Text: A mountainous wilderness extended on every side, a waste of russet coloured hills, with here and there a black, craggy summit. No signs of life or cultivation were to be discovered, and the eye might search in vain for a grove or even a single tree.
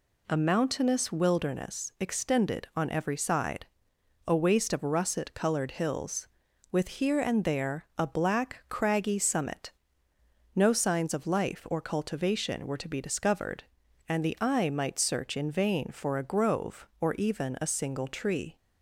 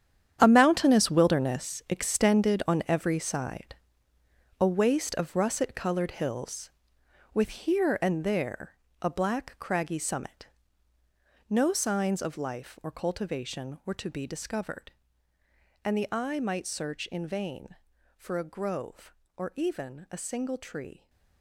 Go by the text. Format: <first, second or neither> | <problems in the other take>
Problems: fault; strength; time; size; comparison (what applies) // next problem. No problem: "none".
first | gets quieter; strong; throughout; 14 dB // pauses between "there" and "a"; slight; at 8.7 s; 0.26 s long